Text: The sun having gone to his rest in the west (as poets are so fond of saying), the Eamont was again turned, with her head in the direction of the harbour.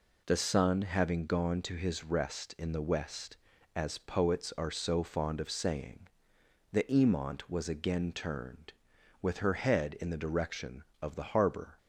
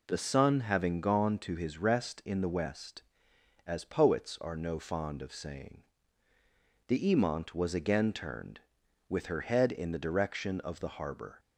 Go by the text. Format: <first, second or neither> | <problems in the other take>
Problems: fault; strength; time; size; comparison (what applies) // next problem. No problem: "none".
first | says "no" for "so"; at 4.5 s